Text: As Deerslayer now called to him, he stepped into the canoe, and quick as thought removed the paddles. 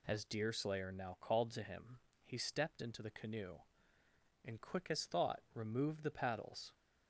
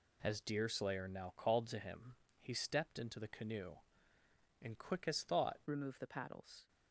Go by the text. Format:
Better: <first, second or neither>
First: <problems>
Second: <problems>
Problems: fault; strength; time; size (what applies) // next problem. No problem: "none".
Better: first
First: none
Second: changes voice at "removed"; from 5.6 s on; 1.0 s long